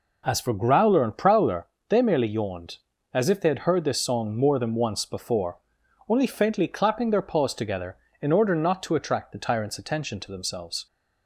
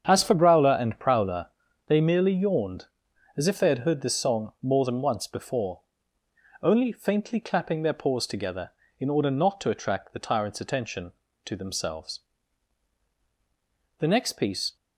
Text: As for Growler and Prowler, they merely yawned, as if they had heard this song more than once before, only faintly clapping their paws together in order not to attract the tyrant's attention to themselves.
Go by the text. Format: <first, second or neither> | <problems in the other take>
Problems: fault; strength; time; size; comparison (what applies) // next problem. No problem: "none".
first | starts louder than the rest; strong; until 1.0 s; 7.5 dB // goes on to say "The next piece"; noticeable; from 13.9 s on; 0.76 s long